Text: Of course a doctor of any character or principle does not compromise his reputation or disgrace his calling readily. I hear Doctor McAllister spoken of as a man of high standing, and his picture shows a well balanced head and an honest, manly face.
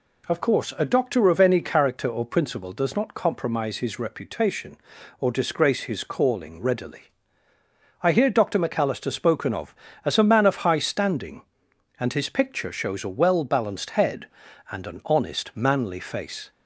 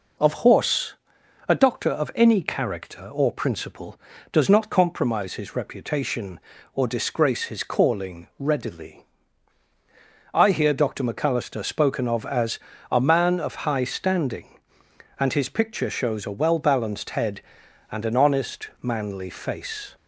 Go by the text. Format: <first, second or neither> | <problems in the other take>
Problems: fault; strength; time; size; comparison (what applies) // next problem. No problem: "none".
first | says "horse" for "course"; at 0.3 s // pauses between "as" and "a"; slight; at 12.5 s; 0.32 s long